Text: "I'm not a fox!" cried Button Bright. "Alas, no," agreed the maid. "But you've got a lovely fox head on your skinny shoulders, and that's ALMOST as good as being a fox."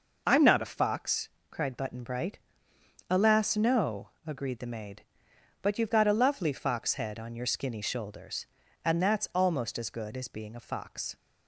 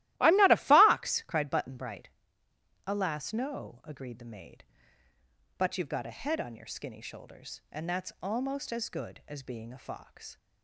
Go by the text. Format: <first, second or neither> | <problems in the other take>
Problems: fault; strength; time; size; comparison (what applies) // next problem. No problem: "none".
first | starts louder than the rest; strong; until 1.1 s; 16 dB // skips "lovely fox"; at 6.1 s